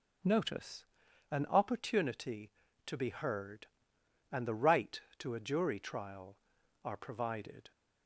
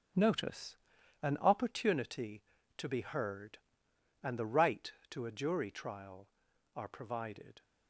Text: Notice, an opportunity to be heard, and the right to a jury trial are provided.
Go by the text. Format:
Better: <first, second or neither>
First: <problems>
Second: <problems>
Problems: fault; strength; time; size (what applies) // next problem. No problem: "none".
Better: first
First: none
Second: gets quieter; strong; throughout; 9 dB